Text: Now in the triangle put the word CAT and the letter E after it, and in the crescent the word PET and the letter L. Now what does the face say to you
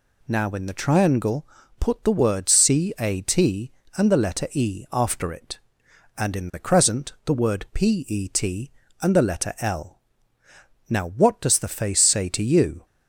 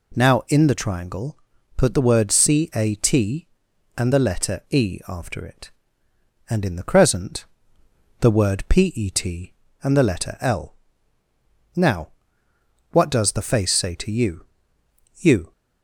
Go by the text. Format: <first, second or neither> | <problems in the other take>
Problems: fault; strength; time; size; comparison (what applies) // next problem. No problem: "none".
first | pauses between "triangle" and "put"; at 1.3 s; 0.40 s long; slight in the first // pauses between "crescent" and "the"; noticeable; at 7.4 s; 0.74 s long // pauses between "Now" and "what"; noticeable; at 12.0 s; 0.82 s long // says "you" twice; at 15.1 s